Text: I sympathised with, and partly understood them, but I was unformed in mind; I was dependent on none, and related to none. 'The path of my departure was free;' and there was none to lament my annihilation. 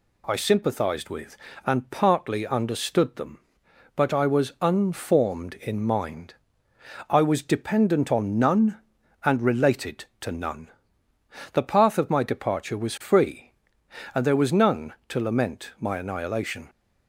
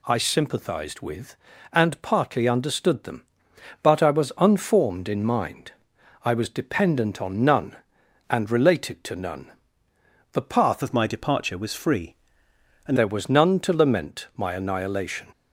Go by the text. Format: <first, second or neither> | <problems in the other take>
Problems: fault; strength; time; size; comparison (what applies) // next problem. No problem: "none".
first | changes voice from "of" to "and"; from 10.8 to 12.9 s; 2.1 s long